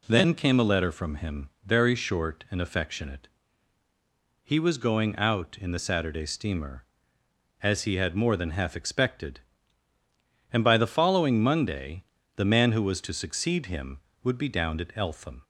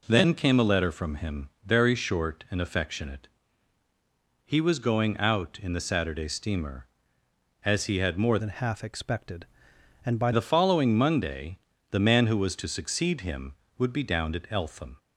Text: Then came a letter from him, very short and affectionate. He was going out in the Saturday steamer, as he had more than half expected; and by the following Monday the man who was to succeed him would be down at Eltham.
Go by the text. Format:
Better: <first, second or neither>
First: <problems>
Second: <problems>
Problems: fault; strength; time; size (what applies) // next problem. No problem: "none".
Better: first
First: pauses between "Monday" and "the"; slight; at 12.0 s; 0.34 s long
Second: changes voice from "than" to "by"; from 8.3 to 10.3 s; 2.0 s long // pauses between "Monday" and "the"; slight; at 11.5 s; 0.34 s long